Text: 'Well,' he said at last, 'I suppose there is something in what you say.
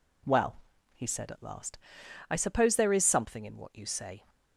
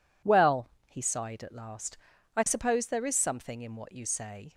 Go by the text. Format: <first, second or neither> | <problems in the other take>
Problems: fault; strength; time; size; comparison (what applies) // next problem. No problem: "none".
first | says "sighed" for "said"; at 1.0 s